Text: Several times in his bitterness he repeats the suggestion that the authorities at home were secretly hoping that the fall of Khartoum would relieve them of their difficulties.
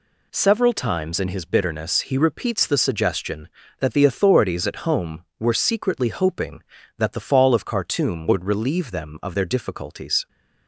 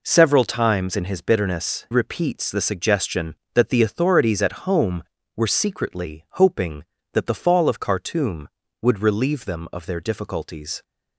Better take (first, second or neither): first